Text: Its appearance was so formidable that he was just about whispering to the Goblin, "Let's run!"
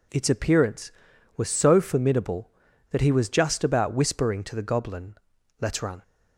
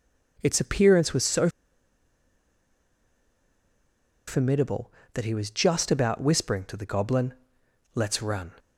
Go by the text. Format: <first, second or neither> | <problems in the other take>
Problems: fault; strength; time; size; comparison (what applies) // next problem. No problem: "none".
first | pauses between "so" and "formidable"; strong; at 1.4 s; 2.7 s long